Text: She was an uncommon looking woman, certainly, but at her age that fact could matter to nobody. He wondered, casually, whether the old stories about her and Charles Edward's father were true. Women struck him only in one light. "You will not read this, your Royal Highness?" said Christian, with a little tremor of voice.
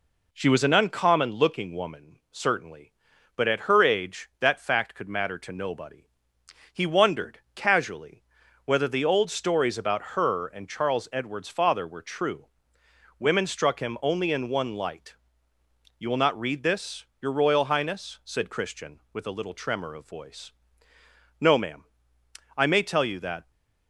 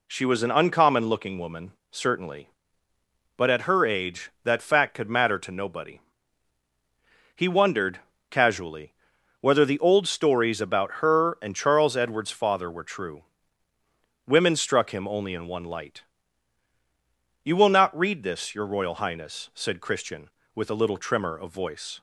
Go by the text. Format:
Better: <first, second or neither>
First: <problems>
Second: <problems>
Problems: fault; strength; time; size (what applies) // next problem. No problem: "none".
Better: second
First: goes on to say "No ma'am I may tell you that"; strong; from 21.4 s on; 2.1 s long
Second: none